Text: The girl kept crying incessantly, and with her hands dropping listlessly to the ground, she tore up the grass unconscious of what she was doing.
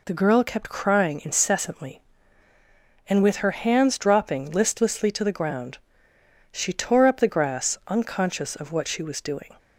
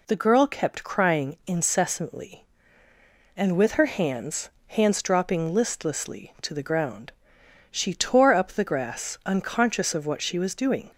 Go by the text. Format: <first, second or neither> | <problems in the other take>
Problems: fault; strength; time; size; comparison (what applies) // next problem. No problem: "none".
first | says "hands" twice; at 4.6 s